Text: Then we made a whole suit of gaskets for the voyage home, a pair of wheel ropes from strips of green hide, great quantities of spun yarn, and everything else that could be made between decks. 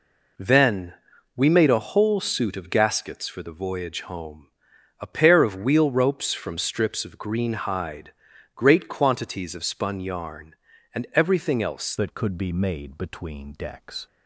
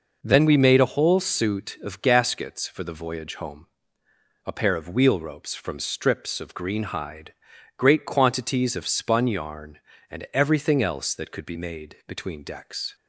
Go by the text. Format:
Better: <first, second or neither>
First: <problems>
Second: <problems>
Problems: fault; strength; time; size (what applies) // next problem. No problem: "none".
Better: second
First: pauses between "Then" and "we"; at 0.9 s; 0.42 s long // changes voice at "that"; from 11.9 s on; 2.1 s long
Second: none